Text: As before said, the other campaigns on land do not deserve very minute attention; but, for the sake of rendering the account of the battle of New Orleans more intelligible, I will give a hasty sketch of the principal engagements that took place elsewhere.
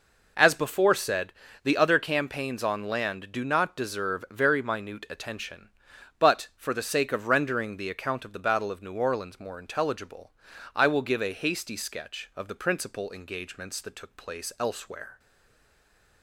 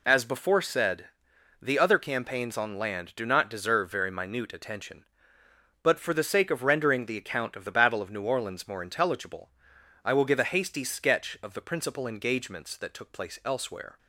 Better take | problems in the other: second | stays silent after the last word; from 15.1 s on; 1.1 s long

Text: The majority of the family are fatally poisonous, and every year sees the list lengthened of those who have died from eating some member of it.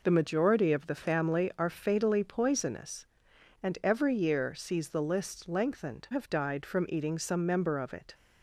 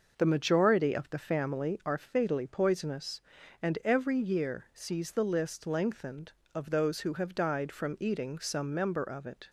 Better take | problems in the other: second | skips "of those who"; at 6.0 s

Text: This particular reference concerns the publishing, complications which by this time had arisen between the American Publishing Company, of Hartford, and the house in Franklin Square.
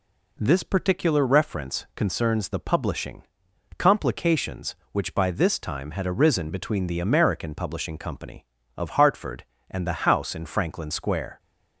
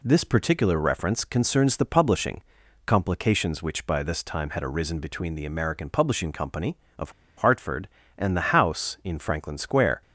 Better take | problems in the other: first | pauses between "of" and "Hartford"; slight; at 7.1 s; 0.26 s long

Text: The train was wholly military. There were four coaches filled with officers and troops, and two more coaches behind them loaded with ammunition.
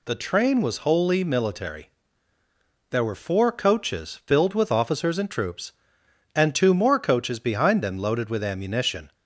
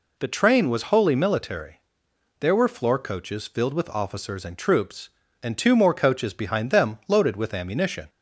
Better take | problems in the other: first | says "floor" for "four"; at 2.6 s

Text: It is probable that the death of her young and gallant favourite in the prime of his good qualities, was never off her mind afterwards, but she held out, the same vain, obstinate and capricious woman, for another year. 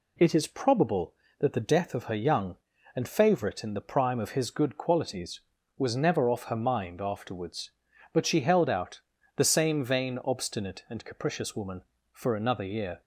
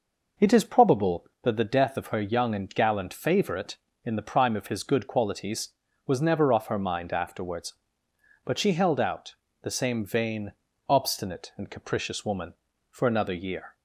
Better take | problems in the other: second | skips "gallant"; at 3.0 s

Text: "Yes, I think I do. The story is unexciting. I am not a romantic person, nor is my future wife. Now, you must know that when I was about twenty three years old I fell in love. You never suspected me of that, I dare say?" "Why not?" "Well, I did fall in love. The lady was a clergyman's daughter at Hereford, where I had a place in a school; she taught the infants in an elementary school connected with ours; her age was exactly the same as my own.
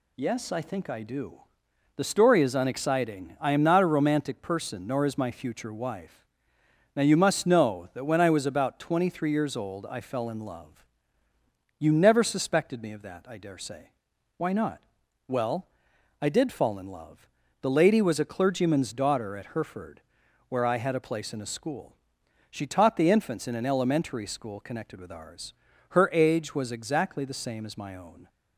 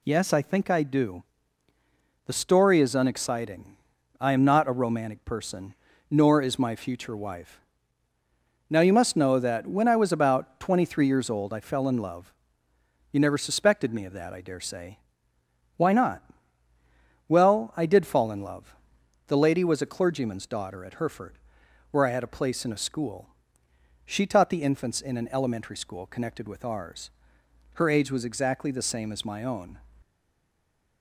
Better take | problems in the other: first | stays silent after the last word; from 30.0 s on; 1.0 s long

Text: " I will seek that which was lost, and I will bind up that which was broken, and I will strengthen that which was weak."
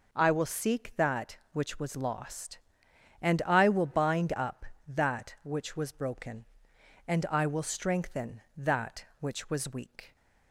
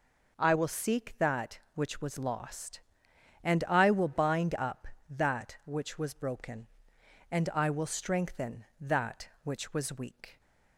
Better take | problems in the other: neither | none

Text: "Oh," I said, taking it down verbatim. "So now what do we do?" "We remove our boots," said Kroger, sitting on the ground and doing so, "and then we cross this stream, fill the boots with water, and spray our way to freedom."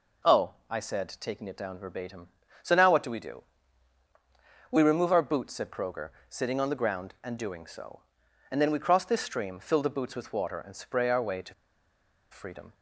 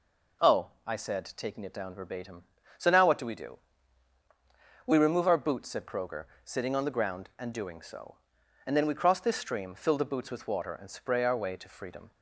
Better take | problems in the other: second | pauses between "to" and "freedom"; noticeable; at 11.5 s; 0.77 s long

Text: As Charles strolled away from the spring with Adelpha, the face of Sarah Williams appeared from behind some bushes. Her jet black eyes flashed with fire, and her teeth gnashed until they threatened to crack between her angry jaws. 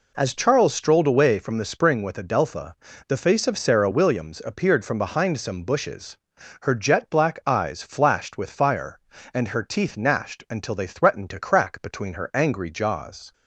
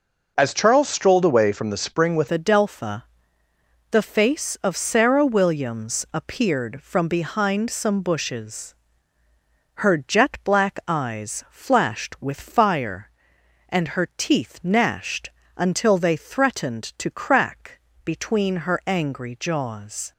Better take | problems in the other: first | changes voice at "Adelpha"; from 2.3 s on; 17.8 s long // pauses between "gnashed" and "until"; slight; at 15.3 s; 0.26 s long // pauses between "crack" and "between"; slight; at 17.8 s; 0.24 s long

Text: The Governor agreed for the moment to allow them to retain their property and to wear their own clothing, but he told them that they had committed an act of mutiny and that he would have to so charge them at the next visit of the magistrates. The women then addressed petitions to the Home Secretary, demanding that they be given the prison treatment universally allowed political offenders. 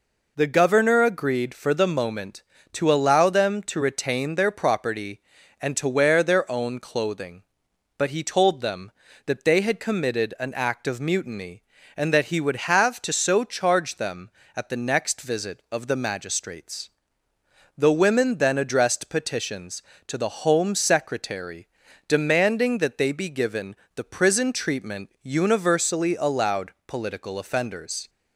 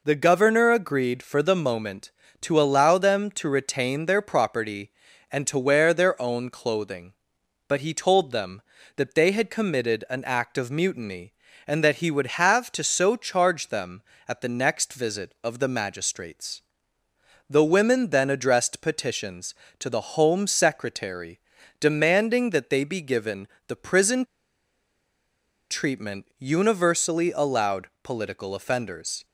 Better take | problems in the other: first | pauses between "given" and "the"; slight; at 23.4 s; 0.20 s long; slight in the first // pauses between "prison" and "treatment"; strong; at 24.2 s; 1.4 s long

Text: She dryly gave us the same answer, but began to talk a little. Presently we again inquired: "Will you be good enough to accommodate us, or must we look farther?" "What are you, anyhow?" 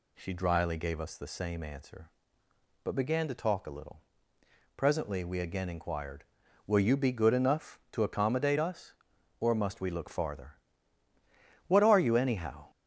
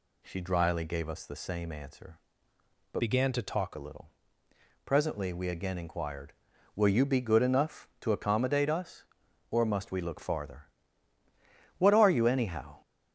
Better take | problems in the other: first | changes voice from "began" to "talk"; from 2.9 to 3.7 s; 0.8 s long

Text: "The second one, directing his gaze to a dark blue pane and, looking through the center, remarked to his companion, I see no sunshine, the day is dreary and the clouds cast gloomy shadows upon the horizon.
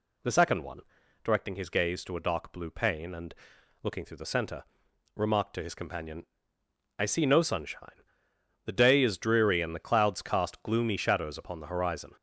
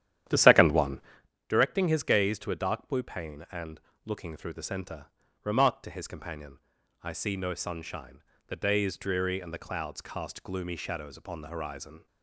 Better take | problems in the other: first | starts louder than the rest; strong; until 1.3 s; 11 dB

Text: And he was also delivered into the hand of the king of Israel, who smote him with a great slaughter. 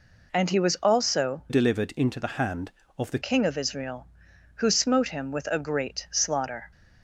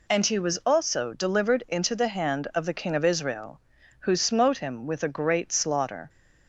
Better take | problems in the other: second | changes voice from "delivered" to "the"; from 1.4 to 3.1 s; 1.7 s long

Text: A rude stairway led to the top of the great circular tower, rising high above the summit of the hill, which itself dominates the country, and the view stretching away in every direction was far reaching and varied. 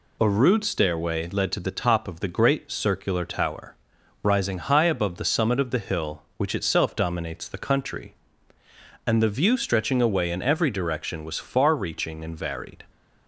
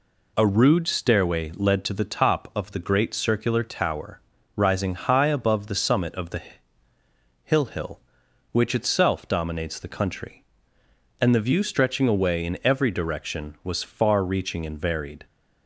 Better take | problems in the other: first | pauses between "the" and "hill"; at 6.4 s; 1.0 s long // says "hill" twice; at 7.6 s

